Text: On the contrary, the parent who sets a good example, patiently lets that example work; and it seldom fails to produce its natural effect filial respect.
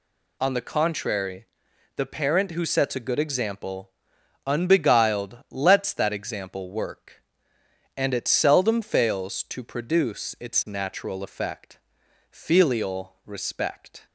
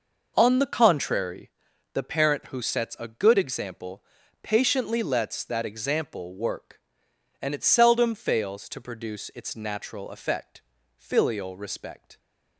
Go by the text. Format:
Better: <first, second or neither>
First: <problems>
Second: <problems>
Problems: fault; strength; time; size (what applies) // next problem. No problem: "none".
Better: second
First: says "unbeguiled" for "patiently"; at 4.4 s // pauses between "effect" and "filial"; noticeable; at 11.7 s; 0.50 s long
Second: pauses between "effect" and "filial"; slight; at 10.6 s; 0.34 s long